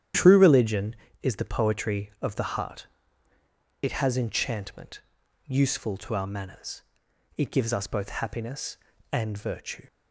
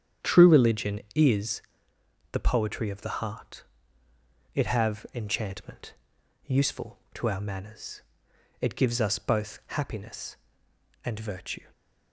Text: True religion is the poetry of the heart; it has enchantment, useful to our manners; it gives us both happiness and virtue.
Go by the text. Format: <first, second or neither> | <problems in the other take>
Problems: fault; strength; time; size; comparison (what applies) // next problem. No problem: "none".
first | starts louder than the rest; strong; until 1.3 s; 9 dB; strong in the first // pauses between "is" and "the"; noticeable; at 1.6 s; 0.70 s long // says "have" for "has"; at 4.6 s // stays silent after the last word; slight; from 11.6 s on; 0.5 s long